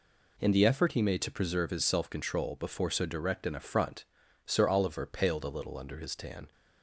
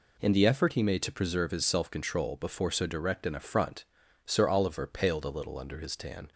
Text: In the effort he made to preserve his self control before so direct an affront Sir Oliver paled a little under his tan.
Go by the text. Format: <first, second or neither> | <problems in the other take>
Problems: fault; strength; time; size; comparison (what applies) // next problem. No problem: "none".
neither | pauses between "affront" and "Sir"; the same in both